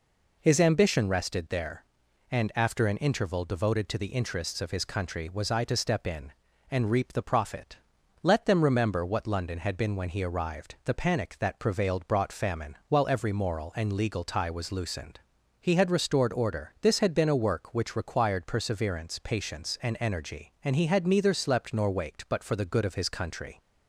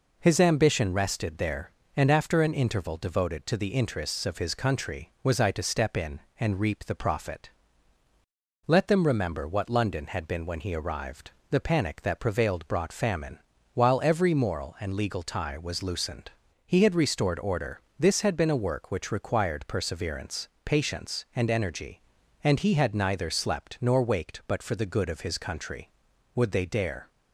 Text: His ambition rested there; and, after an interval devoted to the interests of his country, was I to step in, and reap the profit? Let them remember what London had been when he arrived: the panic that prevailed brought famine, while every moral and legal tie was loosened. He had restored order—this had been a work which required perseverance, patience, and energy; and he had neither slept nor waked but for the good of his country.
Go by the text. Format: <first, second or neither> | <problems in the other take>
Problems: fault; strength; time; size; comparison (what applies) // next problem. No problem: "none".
first | goes on to say "Would they dare"; noticeable; from 26.3 s on; 0.74 s long